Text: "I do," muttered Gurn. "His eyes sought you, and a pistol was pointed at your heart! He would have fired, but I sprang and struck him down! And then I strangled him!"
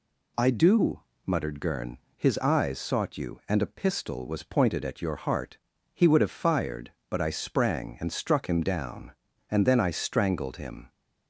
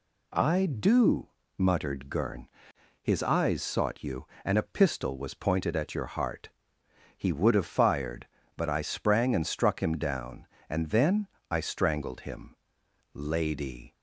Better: first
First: none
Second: pauses between "then" and "I"; slight; at 11.2 s; 0.24 s long // goes on to say "Lady"; noticeable; from 13.1 s on; 0.80 s long

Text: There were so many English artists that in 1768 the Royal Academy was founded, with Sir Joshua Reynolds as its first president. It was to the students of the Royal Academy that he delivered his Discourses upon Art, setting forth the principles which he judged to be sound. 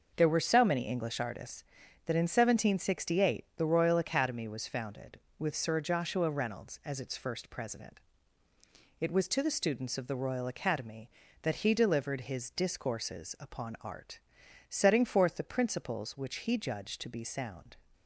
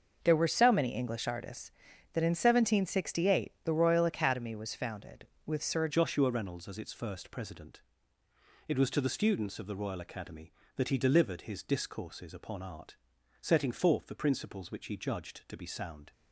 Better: first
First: starts louder than the rest; noticeable; until 1.1 s; 6 dB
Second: starts louder than the rest; until 1.2 s; 6 dB // changes voice at "Joshua"; from 5.8 s on; 10.3 s long

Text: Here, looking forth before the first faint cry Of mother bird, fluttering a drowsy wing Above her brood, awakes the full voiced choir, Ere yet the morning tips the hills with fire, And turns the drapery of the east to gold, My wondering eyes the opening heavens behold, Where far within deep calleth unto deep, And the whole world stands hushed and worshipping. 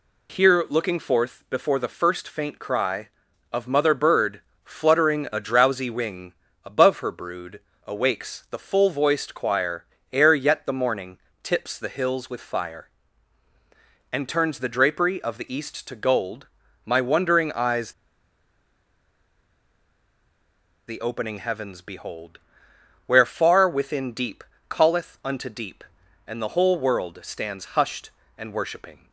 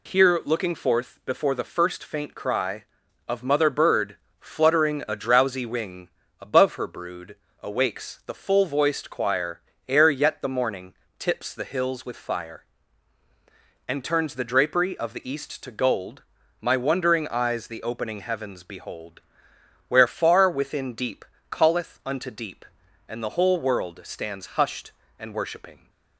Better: second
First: pauses between "wing" and "Above"; slight; at 6.3 s; 0.28 s long // pauses between "morning" and "tips"; slight; at 11.1 s; 0.24 s long // pauses between "eyes" and "the"; strong; at 17.9 s; 2.9 s long // pauses between "deep" and "calleth"; slight; at 24.4 s; 0.28 s long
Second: pauses between "wing" and "Above"; slight; at 6.1 s; 0.28 s long // pauses between "morning" and "tips"; slight; at 10.9 s; 0.24 s long // pauses between "deep" and "calleth"; slight; at 21.2 s; 0.28 s long

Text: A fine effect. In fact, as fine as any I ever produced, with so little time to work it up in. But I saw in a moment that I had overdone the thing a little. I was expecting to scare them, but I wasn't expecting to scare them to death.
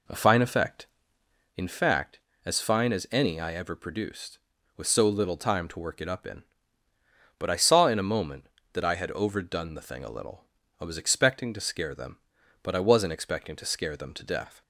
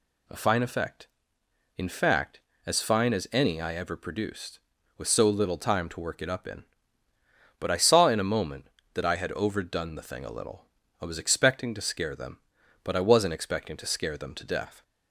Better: second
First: starts louder than the rest; slight; until 1.5 s; 3.5 dB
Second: none

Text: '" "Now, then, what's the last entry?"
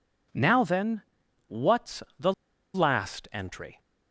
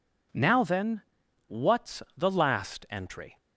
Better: second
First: pauses between "what's" and "the"; slight; at 2.0 s; 0.16 s long // pauses between "the" and "last"; at 2.3 s; 0.42 s long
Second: none

